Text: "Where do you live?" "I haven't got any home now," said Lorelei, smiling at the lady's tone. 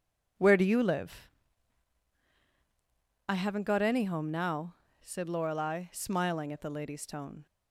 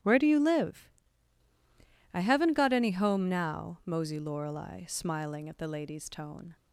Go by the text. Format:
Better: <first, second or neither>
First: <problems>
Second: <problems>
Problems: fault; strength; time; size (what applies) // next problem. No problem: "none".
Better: first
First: none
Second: starts louder than the rest; strong; until 2.2 s; 10.5 dB // says "mosey" for "said"; at 3.8 s